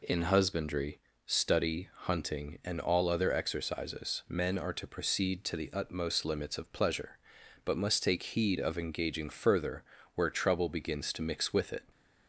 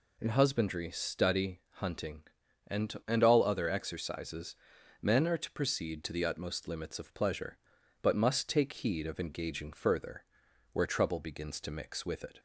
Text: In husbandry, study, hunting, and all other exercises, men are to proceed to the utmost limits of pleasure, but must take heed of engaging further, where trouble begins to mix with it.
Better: first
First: none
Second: says "and" twice; at 3.0 s

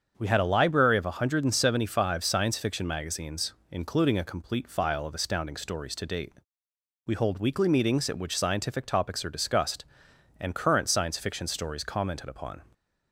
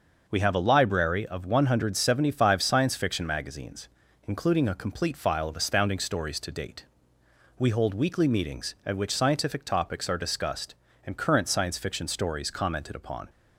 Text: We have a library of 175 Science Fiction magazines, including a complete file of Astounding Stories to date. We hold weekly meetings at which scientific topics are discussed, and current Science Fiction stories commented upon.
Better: second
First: starts louder than the rest; until 1.1 s; 7 dB // says "had" for "have"; at 0.2 s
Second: none

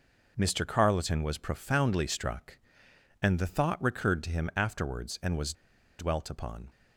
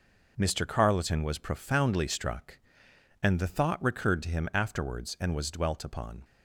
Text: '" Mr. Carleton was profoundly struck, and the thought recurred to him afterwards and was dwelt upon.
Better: second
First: pauses between "was" and "dwelt"; at 5.5 s; 0.45 s long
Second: none

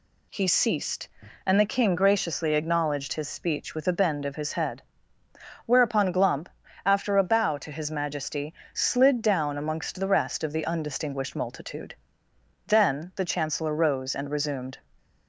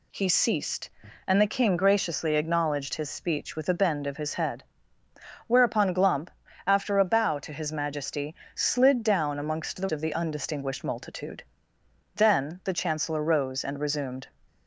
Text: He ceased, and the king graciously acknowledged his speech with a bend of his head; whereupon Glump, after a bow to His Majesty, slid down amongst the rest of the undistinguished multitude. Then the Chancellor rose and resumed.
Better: first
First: none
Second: skips "rest"; at 9.8 s

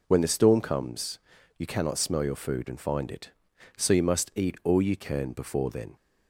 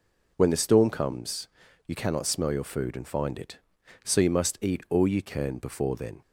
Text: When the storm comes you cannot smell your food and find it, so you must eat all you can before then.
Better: neither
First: pauses between "comes" and "you"; at 1.1 s; 0.38 s long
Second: pauses between "comes" and "you"; at 1.4 s; 0.38 s long

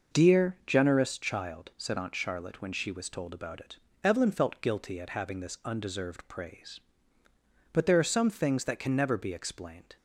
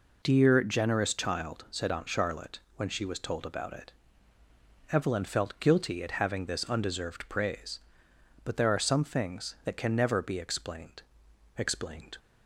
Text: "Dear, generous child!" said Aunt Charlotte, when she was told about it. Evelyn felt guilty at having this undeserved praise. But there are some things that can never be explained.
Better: first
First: none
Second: says "explained" twice; at 11.5 s

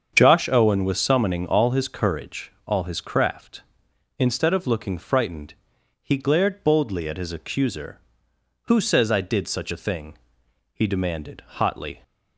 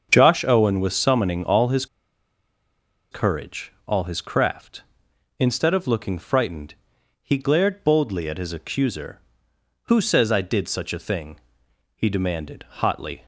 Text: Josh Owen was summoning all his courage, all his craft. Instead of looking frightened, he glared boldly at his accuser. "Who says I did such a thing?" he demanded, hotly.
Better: first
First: starts louder than the rest; strong; until 1.1 s; 7.5 dB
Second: starts louder than the rest; strong; until 1.1 s; 7 dB // pauses between "his" and "courage"; strong; at 1.8 s; 1.2 s long

